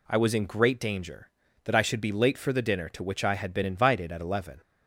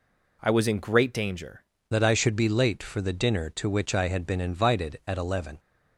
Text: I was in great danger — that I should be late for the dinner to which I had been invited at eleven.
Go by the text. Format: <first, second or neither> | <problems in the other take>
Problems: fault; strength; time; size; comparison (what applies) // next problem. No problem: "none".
first | changes voice at "that"; from 1.8 s on; 3.7 s long